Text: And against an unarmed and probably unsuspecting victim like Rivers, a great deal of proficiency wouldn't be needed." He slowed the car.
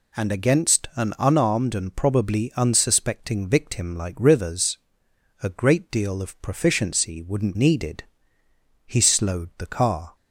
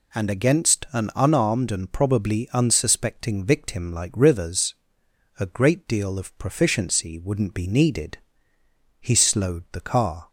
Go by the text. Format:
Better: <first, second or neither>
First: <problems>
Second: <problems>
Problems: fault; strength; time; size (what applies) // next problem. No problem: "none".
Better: second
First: skips "be"; at 7.5 s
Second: none